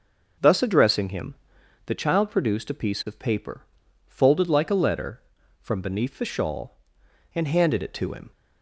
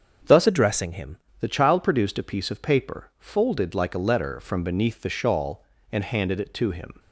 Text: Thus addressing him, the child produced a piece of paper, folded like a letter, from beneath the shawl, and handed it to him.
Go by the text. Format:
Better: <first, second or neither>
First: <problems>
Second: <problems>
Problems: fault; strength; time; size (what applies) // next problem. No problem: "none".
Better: first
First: none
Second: starts louder than the rest; until 1.5 s; 7 dB // changes voice from "addressing" to "him"; from 0.4 to 1.1 s; 0.7 s long